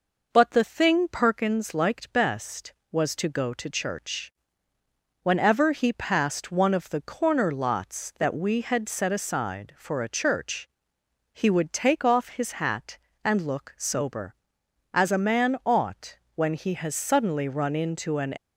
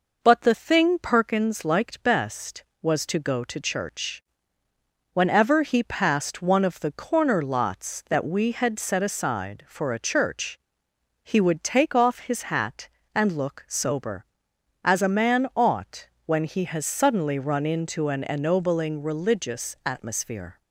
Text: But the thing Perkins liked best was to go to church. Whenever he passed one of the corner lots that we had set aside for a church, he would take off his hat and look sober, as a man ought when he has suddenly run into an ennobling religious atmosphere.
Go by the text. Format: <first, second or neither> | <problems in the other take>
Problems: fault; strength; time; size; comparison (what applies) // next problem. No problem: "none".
second | pauses between "ought" and "when"; slight; at 16.1 s; 0.20 s long; slight in the second // stops before "ennobling religious atmosphere"; at 18.3 s